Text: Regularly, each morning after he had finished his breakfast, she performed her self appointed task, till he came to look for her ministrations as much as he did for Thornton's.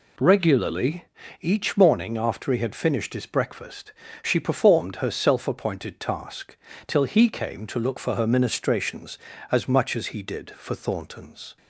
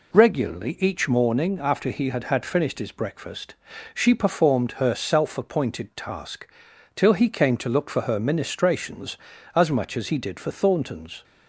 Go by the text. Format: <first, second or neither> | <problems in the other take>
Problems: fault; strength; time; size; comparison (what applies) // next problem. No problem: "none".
first | says "had" twice; at 2.2 s